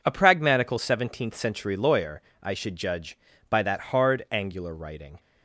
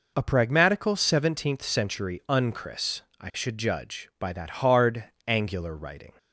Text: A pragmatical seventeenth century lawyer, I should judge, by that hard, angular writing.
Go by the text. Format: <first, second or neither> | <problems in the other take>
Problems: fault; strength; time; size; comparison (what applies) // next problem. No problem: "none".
first | says "unchris" for "lawyer"; at 2.2 s